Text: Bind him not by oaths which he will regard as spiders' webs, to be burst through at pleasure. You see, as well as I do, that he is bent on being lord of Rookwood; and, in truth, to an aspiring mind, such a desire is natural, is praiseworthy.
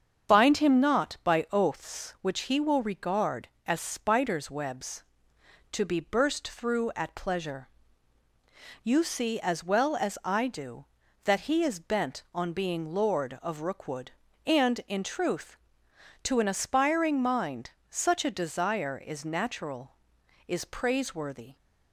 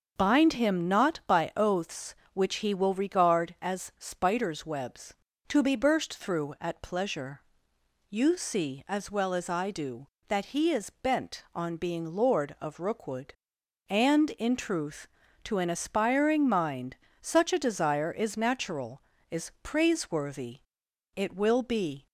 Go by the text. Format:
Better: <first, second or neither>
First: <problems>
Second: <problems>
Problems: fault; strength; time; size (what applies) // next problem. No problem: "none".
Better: first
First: starts louder than the rest; strong; until 1.3 s; 7.5 dB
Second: starts louder than the rest; until 1.1 s; 6.5 dB // goes on to say "It will be"; noticeable; from 21.1 s on; 0.92 s long